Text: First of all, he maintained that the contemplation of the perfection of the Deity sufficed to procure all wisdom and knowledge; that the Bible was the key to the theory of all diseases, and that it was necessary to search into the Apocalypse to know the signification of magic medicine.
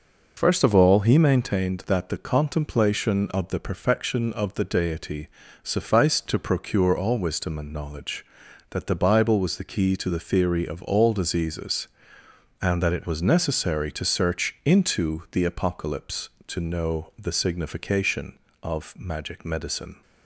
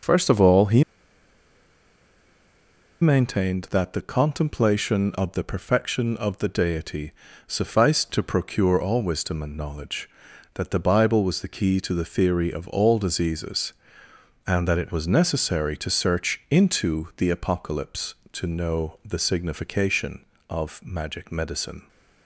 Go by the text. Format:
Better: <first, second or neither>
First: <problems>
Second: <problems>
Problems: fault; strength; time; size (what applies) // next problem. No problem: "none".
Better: first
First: pauses between "Deity" and "sufficed"; at 5.2 s; 0.38 s long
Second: pauses between "he" and "maintained"; strong; at 0.8 s; 2.1 s long // pauses between "Deity" and "sufficed"; at 7.0 s; 0.38 s long